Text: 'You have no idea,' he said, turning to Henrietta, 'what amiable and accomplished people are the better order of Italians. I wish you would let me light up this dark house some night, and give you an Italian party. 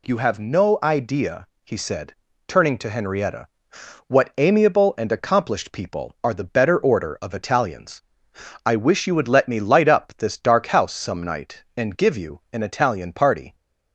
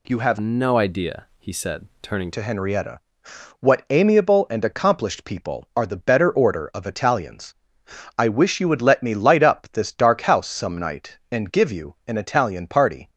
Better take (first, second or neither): first